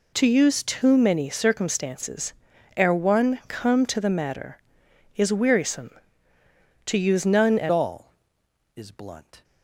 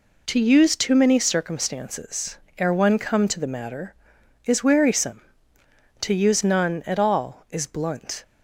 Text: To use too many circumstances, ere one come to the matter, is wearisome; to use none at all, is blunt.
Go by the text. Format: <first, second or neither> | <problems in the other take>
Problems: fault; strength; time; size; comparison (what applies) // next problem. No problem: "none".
second | changes voice at "all"; from 7.7 s on; 1.7 s long